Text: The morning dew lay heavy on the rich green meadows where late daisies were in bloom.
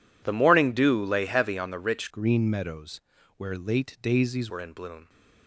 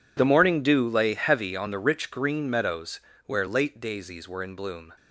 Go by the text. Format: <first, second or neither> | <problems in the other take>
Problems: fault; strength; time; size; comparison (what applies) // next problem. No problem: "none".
second | changes voice from "green" to "daisies"; from 2.1 to 4.5 s; 2.4 s long // pauses between "meadows" and "where"; slight; at 3.0 s; 0.36 s long; slight in the second